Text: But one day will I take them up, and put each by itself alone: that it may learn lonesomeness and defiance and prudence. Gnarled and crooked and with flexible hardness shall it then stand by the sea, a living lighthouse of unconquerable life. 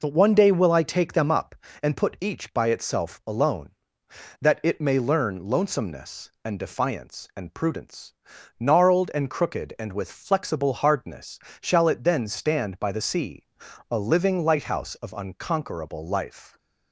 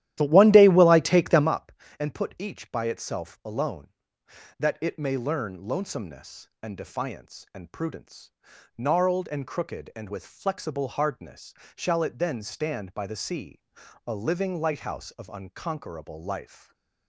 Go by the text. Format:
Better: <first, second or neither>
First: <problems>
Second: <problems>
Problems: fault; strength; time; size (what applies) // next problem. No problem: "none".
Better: first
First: pauses between "hardness" and "shall"; slight; at 11.3 s; 0.22 s long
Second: starts louder than the rest; strong; until 1.6 s; 13 dB // pauses between "hardness" and "shall"; slight; at 11.5 s; 0.22 s long // stays silent after the last word; slight; from 16.4 s on; 0.6 s long